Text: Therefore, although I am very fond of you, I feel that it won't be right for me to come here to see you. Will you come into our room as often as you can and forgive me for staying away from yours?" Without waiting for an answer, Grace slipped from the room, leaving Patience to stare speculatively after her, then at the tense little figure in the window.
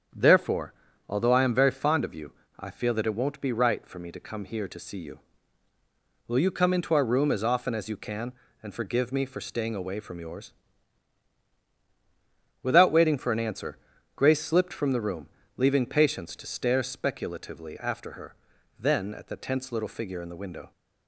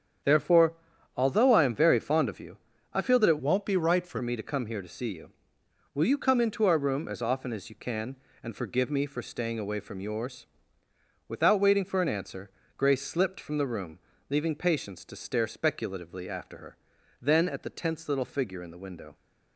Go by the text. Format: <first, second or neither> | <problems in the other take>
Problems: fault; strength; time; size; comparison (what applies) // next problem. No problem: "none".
first | starts louder than the rest; strong; until 1.6 s; 8.5 dB; strong in the first // changes voice from "won't" to "for"; from 3.3 to 4.1 s; 0.8 s long